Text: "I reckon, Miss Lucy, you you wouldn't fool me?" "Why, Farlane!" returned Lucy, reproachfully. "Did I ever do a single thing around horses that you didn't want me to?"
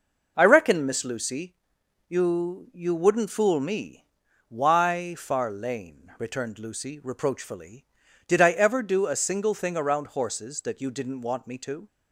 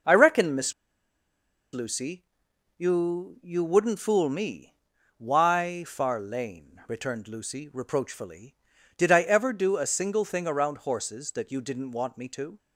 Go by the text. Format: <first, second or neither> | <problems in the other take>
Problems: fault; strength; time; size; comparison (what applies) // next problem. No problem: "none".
first | pauses between "Miss" and "Lucy"; at 0.7 s; 1.0 s long